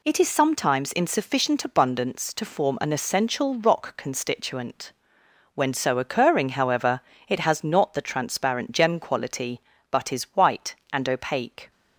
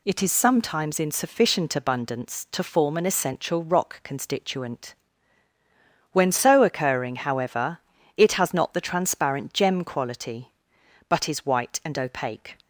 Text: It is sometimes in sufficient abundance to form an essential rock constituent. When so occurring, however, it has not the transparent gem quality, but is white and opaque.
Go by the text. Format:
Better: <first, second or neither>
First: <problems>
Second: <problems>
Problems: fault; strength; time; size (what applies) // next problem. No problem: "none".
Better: neither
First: none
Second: none